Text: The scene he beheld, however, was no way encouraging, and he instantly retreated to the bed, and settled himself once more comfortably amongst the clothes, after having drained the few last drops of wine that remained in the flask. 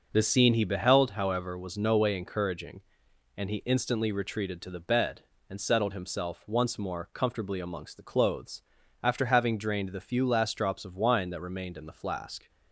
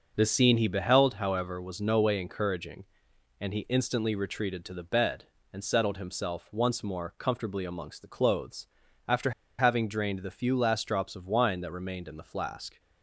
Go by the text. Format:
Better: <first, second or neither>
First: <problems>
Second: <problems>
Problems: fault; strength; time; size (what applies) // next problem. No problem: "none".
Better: first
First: none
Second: pauses between "after" and "having"; slight; at 9.3 s; 0.26 s long